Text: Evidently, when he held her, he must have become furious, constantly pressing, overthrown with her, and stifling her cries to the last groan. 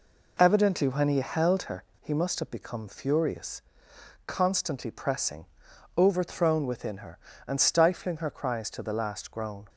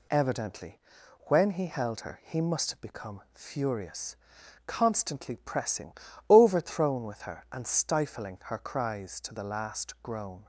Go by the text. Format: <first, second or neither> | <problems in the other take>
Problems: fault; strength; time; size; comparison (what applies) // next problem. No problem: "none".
second | says "within" for "with"; at 6.6 s